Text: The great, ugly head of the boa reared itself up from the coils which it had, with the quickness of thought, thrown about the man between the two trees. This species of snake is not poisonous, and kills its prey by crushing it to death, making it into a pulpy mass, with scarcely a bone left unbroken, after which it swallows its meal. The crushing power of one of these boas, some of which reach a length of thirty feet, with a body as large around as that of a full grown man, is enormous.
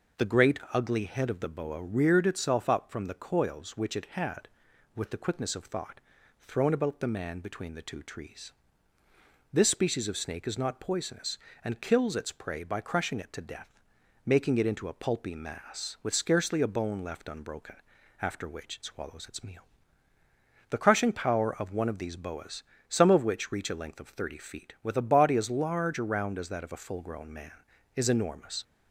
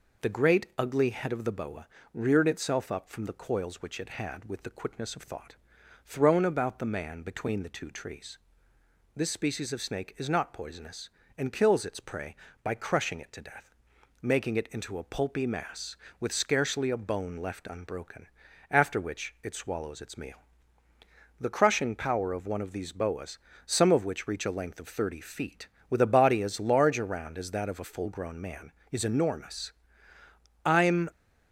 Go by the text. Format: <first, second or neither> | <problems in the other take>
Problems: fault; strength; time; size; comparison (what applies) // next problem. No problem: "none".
first | pauses between "boa" and "reared"; slight; at 1.8 s; 0.26 s long // goes on to say "I'm"; slight; from 30.6 s on; 0.44 s long